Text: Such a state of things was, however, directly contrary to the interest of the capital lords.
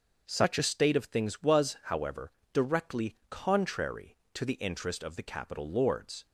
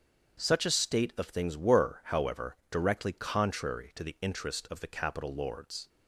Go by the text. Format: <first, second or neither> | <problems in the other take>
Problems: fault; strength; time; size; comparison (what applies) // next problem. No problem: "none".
first | starts louder than the rest; strong; until 1.4 s; 7.5 dB; also in the first // says "were" for "was"; at 1.5 s